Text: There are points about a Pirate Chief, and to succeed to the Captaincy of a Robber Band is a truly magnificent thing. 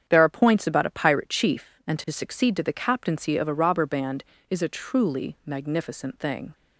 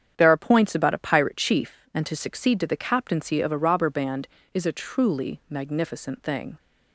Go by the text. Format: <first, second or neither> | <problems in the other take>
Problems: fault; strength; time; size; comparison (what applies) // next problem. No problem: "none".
neither | starts louder than the rest; strong; the same in both